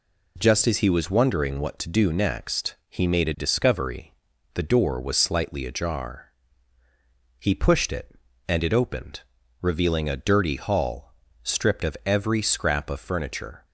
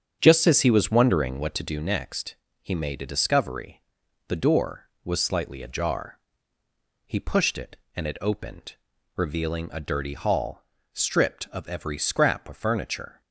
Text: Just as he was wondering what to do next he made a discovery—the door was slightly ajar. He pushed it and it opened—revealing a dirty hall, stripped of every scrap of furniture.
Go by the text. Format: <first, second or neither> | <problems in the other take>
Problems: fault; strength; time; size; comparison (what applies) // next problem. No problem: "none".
first | starts louder than the rest; strong; until 1.4 s; 8 dB // pauses between "next" and "he"; slight; at 2.3 s; 0.26 s long